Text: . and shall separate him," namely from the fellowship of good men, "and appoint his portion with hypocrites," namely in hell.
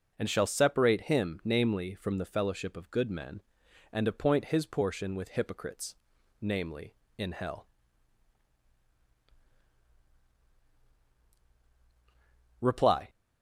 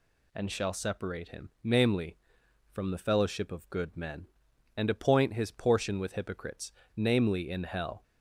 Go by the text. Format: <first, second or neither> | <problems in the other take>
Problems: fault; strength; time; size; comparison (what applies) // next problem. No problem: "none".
second | goes on to say "Reply"; slight; from 12.6 s on; 0.48 s long